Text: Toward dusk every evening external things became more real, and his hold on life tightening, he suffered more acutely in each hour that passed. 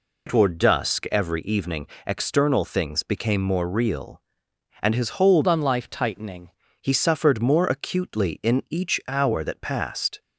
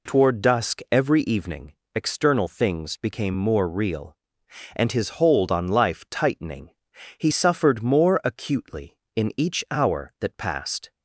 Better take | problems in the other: second | pauses between "evening" and "external"; slight; at 1.8 s; 0.18 s long; slight in the second // changes voice from "on" to "tightening"; from 5.4 to 6.4 s; 1.0 s long

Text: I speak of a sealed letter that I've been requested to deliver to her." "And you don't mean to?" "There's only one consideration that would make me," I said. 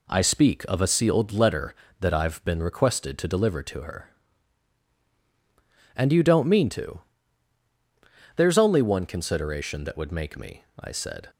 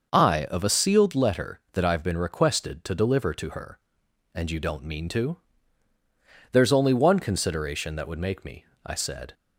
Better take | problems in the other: first | skips "speak"; at 0.4 s

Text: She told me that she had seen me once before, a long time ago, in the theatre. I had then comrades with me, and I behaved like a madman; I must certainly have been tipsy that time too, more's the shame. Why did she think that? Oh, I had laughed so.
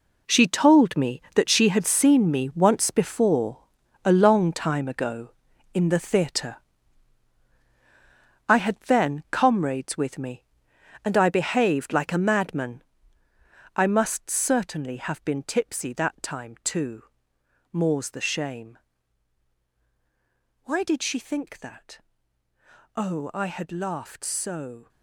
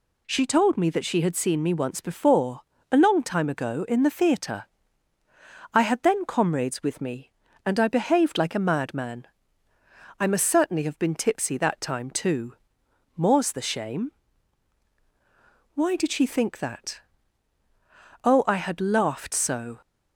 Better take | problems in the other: second | gets quieter; strong; throughout; 12 dB

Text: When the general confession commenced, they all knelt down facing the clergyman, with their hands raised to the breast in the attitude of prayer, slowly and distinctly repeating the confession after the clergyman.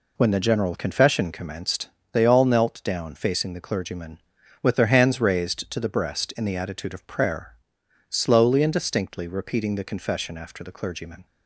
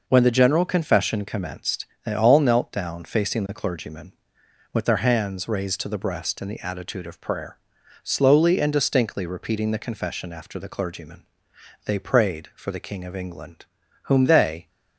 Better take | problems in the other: first | goes on to say "They prayed for the King of England whom they"; strong; from 11.8 s on; 2.8 s long

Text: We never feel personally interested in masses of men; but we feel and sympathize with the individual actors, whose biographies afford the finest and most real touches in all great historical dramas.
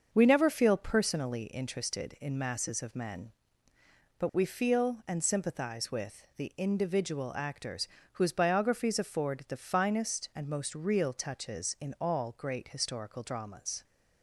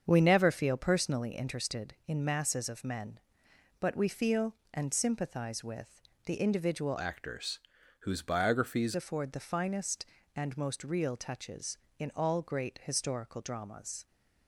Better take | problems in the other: first | starts louder than the rest; until 1.0 s; 7 dB; also in the first // pauses between "with" and "the"; slight; at 5.9 s; 0.28 s long // changes voice from "actors" to "biographies"; from 6.9 to 8.9 s; 2.0 s long

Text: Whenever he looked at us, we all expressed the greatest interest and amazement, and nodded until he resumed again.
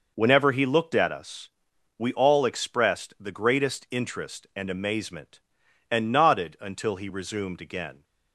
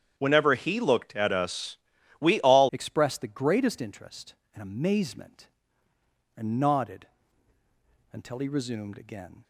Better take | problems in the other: first | starts louder than the rest; strong; until 1.1 s; 9 dB // changes voice at "expressed"; from 2.7 s on; 6.7 s long // pauses between "nodded" and "until"; at 7.0 s; 1.0 s long

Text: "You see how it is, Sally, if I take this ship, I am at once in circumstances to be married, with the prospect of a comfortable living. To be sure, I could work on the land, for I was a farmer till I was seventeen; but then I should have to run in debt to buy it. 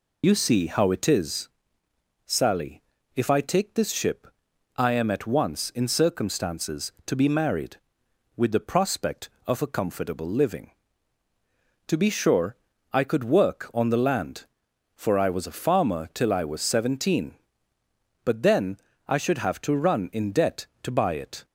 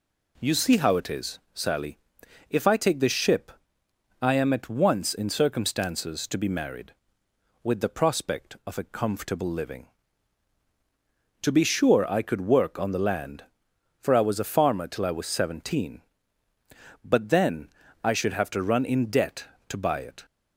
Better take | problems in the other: second | loses the start of "You"; at 0.2 s; 55 ms // pauses between "then" and "I"; slight; at 18.7 s; 0.30 s long; slight in the second

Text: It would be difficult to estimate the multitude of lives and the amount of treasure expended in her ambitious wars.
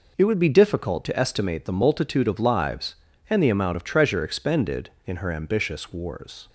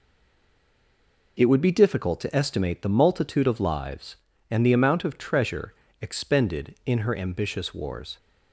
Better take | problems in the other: first | stays silent before the first word; noticeable; until 1.3 s; 1.3 s long // pauses between "treasure" and "expended"; slight; at 5.7 s; 0.26 s long

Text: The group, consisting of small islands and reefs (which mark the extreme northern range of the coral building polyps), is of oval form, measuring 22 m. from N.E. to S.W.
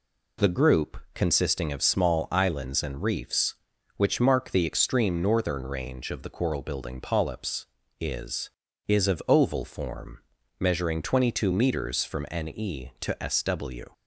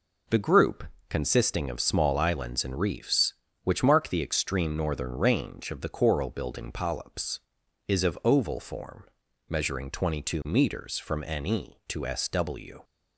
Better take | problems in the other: second | says "is" twice; at 8.8 s

